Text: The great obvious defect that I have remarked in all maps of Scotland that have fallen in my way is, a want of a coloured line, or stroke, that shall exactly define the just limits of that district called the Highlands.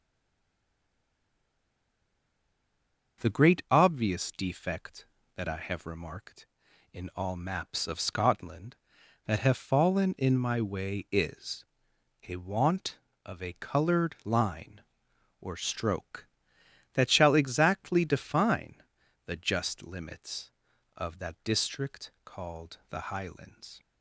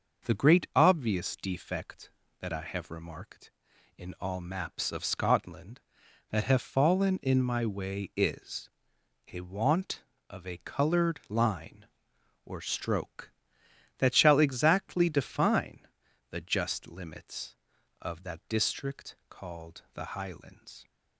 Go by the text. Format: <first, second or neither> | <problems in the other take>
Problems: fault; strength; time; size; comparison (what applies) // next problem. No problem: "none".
second | stays silent before the first word; strong; until 3.2 s; 3.2 s long // starts louder than the rest; noticeable; until 4.2 s; 6 dB; noticeable in the second // pauses between "define" and "the"; noticeable; at 18.7 s; 0.50 s long; noticeable in the second